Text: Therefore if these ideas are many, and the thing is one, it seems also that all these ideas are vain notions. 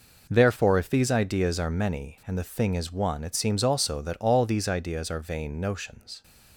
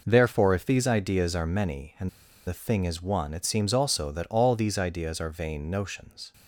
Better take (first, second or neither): first